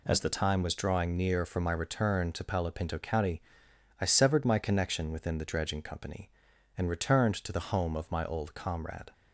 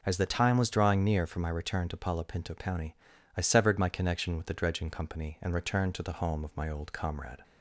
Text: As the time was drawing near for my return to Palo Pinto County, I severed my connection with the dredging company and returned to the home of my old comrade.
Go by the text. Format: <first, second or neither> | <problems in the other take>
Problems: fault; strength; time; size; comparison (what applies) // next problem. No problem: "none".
second | says "within" for "with"; at 5.1 s